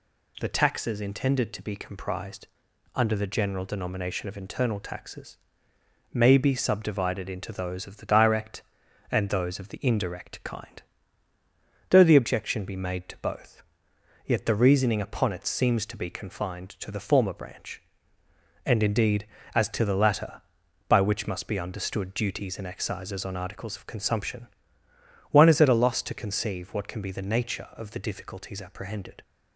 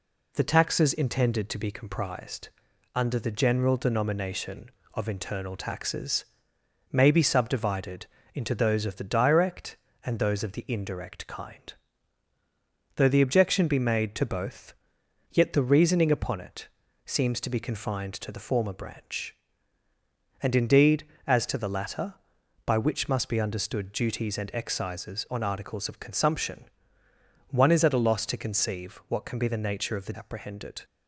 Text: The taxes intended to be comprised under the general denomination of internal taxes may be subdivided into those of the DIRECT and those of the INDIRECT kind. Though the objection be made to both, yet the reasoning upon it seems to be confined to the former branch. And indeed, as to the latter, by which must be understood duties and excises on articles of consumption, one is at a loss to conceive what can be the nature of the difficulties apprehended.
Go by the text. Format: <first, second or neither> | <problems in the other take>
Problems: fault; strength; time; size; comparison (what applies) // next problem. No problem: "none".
first | pauses between "comprised" and "under"; noticeable; at 2.4 s; 0.46 s long; noticeable in the first // pauses between "taxes" and "may"; noticeable; at 6.2 s; 0.66 s long; noticeable in the first // pauses between "subdivided" and "into"; slight; at 8.0 s; 0.26 s long // pauses between "it" and "seems"; at 16.6 s; 0.38 s long // skips "difficulties"; at 30.1 s